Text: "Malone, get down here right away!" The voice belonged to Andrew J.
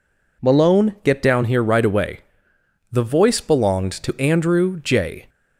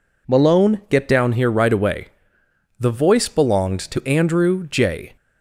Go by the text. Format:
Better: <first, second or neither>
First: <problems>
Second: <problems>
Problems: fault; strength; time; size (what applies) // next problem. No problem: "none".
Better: neither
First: none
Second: none